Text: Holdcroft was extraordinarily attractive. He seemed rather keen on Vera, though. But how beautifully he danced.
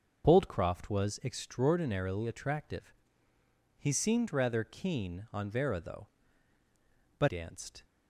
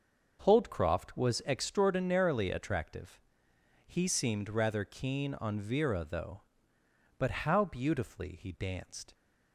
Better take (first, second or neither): second